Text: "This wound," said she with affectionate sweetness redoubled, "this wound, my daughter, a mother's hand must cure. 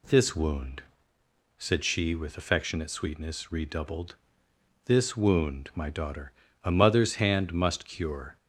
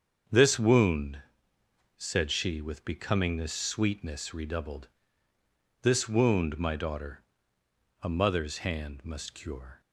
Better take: first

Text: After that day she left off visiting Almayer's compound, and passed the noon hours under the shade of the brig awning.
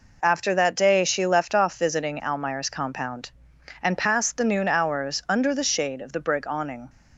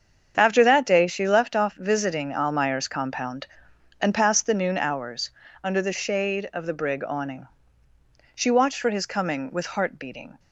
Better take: first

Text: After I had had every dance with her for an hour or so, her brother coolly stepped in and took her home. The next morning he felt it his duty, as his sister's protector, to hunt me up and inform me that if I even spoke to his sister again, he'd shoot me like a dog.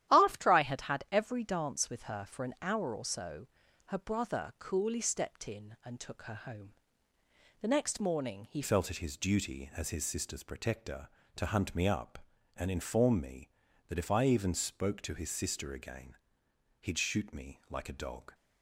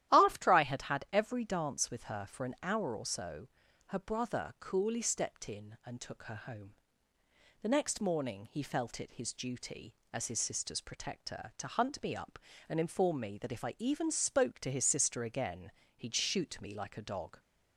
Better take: second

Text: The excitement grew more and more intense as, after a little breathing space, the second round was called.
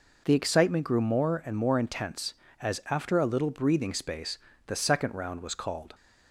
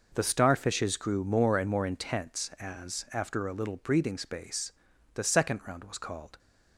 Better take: first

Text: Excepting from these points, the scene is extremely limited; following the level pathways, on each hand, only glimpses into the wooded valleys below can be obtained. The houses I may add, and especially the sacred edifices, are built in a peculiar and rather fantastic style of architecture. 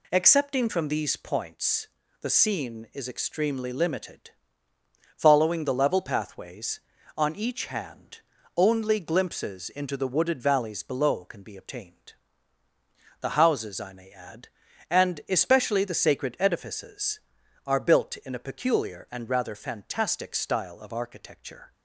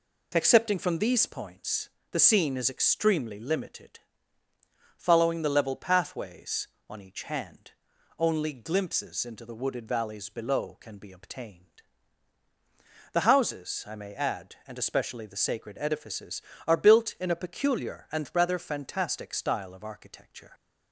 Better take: neither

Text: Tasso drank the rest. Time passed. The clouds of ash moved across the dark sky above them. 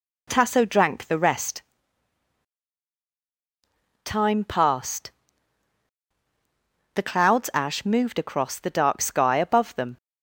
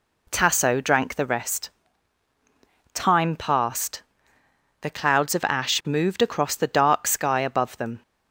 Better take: second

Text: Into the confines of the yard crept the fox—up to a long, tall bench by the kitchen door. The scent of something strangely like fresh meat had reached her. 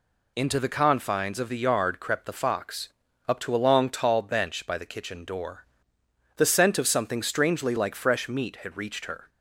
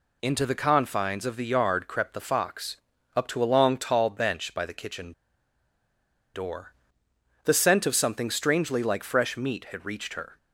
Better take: first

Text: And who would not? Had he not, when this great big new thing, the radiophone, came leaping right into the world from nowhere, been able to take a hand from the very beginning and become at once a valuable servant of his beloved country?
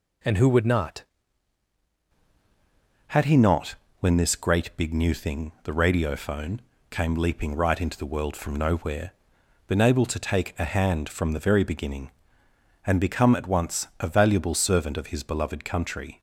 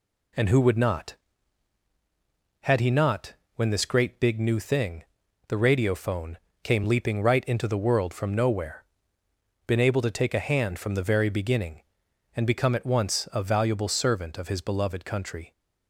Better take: second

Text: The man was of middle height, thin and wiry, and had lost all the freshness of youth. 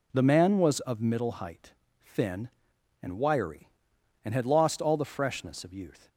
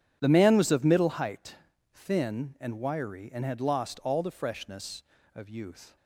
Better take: neither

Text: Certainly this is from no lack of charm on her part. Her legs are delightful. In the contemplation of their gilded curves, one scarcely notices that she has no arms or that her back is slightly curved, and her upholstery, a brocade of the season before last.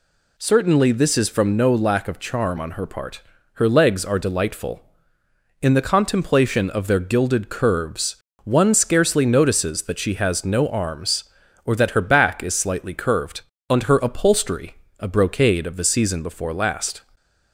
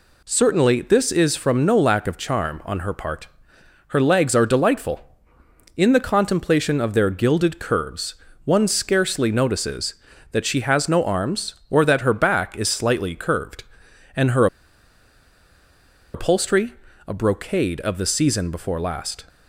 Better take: first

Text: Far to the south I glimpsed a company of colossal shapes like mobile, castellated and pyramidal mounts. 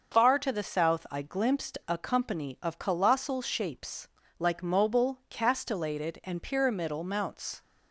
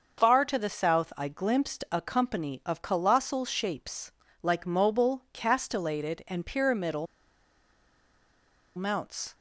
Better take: first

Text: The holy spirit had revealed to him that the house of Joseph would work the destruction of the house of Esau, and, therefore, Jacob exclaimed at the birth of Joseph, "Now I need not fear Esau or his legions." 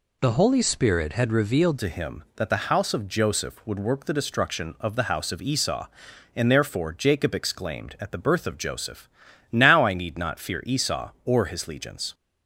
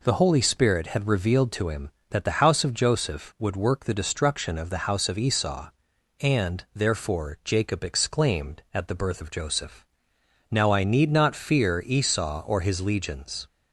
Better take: second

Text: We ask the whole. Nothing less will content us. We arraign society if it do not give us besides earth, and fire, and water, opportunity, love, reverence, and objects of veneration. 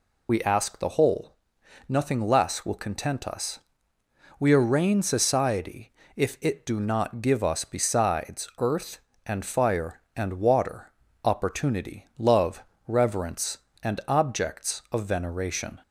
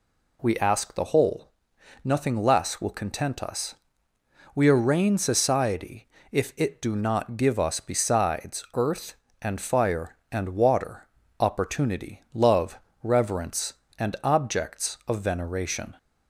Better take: second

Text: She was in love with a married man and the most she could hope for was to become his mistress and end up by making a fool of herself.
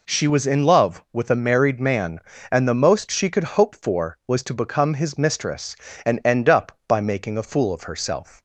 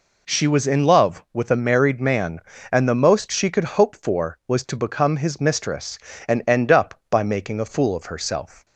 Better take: neither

